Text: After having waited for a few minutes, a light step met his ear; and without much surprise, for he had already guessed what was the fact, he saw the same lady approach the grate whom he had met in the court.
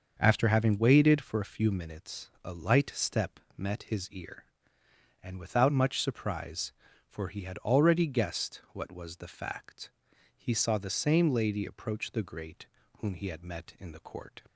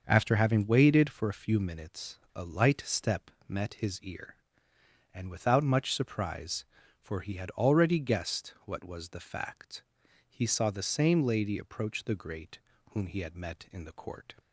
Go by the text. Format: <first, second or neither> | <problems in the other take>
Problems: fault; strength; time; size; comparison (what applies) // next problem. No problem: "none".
neither | starts louder than the rest; the same in both // pauses between "step" and "met"; slight; the same in both // pauses between "grate" and "whom"; slight; the same in both